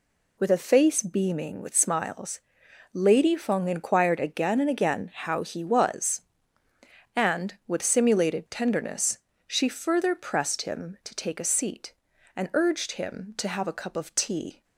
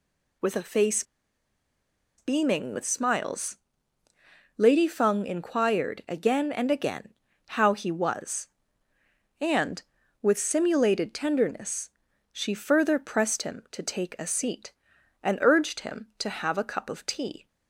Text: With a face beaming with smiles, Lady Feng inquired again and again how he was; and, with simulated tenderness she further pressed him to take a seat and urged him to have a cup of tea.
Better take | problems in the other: first | pauses between "face" and "beaming"; at 1.0 s; 1.1 s long // pauses between "again" and "how"; slight; at 7.1 s; 0.34 s long // pauses between "tenderness" and "she"; at 11.8 s; 0.42 s long; slight in the first

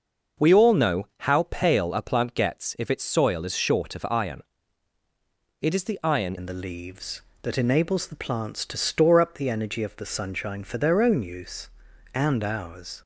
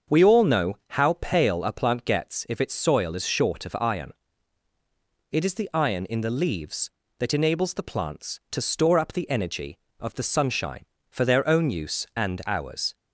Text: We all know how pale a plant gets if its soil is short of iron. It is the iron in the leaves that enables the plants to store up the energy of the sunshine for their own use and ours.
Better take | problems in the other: second | starts louder than the rest; noticeable; until 1.5 s; 6 dB; also in the second // changes voice at "in"; from 6.3 s on; 6.7 s long

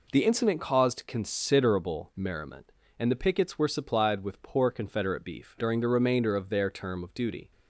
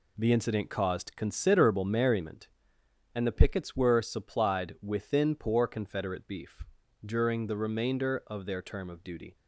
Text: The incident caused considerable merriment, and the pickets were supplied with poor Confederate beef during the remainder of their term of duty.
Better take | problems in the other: first | says "within" for "with"; at 4.8 s // pauses between "beef" and "during"; at 6.6 s; 0.40 s long

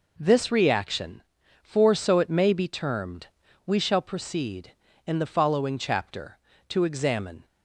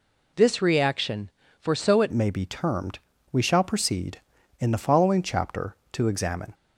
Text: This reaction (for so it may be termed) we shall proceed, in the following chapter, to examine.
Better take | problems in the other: first | changes voice at "may"; from 2.1 s on; 4.4 s long

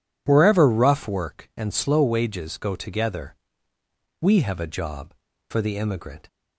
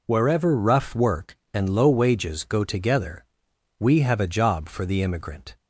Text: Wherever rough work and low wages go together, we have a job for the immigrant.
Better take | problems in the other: second | says "slow" for "low"; at 1.7 s

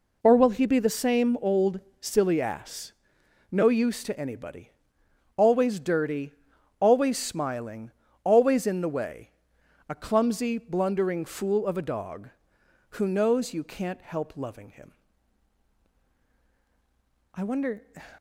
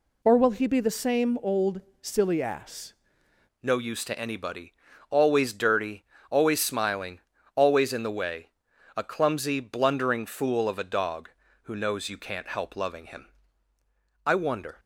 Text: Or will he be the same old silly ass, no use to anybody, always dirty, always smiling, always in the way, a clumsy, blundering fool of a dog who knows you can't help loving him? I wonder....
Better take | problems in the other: first | pauses between "old" and "silly"; slight; at 1.7 s; 0.22 s long; slight in the first // changes voice at "no"; from 3.6 s on; 11.1 s long

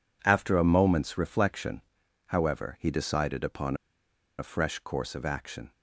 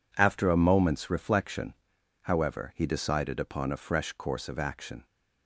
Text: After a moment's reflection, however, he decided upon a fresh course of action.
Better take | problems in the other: second | pauses between "upon" and "a"; noticeable; at 3.7 s; 0.62 s long

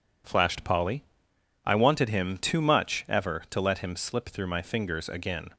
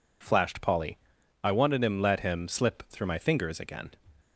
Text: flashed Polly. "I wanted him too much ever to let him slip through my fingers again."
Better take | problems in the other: first | skips "too much ever to"; at 1.9 s

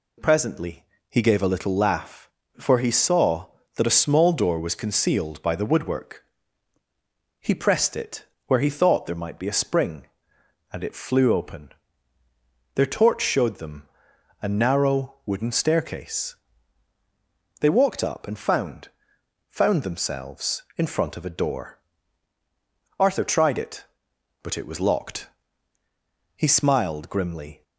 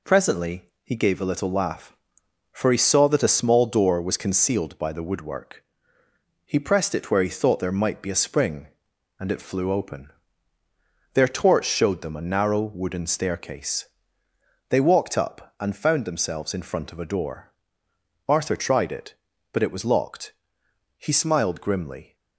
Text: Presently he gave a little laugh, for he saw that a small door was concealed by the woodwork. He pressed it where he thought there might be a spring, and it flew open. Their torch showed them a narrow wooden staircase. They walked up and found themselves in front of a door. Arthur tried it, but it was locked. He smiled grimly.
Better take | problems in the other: second | pauses between "Presently" and "he"; slight; at 0.8 s; 0.26 s long; slight in the second // pauses between "it" and "where"; slight; at 8.2 s; 0.22 s long // pauses between "them" and "a"; noticeable; at 13.8 s; 0.58 s long // says "found" twice; at 19.4 s

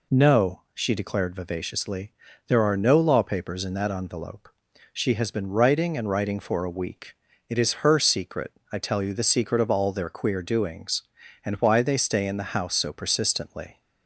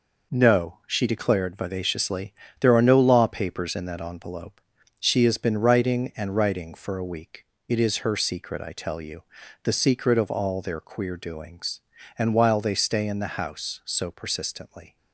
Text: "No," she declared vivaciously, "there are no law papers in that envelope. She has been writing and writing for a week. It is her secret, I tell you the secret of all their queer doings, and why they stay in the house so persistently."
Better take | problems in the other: first | pauses between "you" and "the"; at 9.2 s; 0.40 s long // says "while" for "why"; at 12.3 s

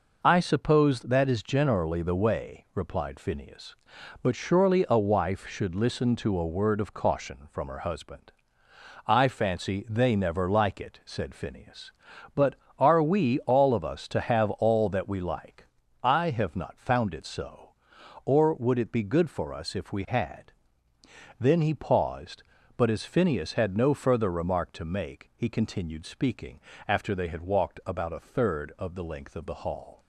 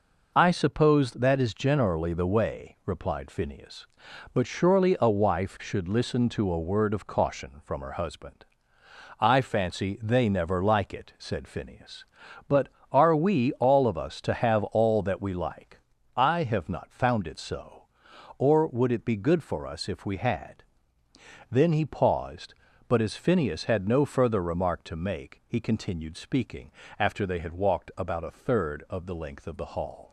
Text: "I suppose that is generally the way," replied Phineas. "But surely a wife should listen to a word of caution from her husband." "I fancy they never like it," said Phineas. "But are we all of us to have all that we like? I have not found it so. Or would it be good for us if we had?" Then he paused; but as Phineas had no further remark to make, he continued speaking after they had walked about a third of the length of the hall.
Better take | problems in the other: neither | pauses between "speaking" and "after"; slight; the same in both

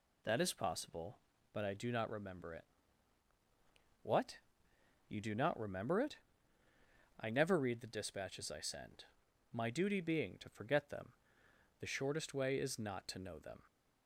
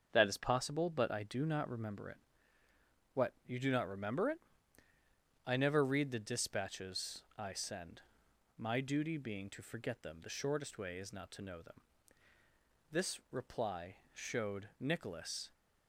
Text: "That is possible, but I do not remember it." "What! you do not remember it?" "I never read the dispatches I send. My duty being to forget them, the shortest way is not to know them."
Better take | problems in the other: first | starts louder than the rest; until 1.1 s; 6.5 dB // pauses between "dispatches" and "I"; slight; at 7.2 s; 0.16 s long // goes on to say "This reply showed Nicholas"; strong; from 12.8 s on; 2.6 s long

